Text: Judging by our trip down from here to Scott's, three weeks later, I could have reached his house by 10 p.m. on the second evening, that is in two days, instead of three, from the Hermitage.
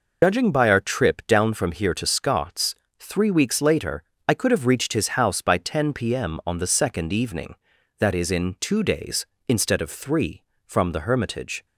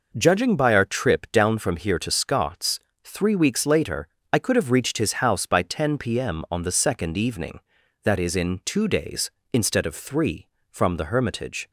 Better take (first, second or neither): second